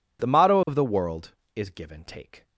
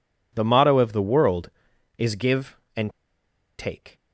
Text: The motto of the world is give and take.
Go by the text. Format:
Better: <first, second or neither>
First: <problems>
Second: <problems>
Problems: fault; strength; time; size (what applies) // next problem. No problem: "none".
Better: first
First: none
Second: pauses between "and" and "take"; noticeable; at 2.8 s; 0.69 s long